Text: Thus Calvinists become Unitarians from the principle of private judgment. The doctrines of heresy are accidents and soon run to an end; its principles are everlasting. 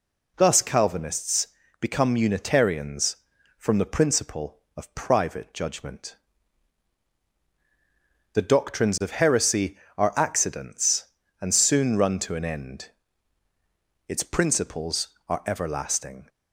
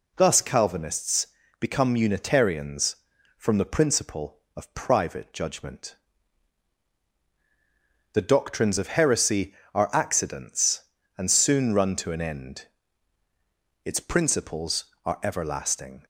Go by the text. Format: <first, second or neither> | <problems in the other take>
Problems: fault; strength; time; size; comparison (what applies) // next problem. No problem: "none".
neither | pauses between "Calvinists" and "become"; slight; the same in both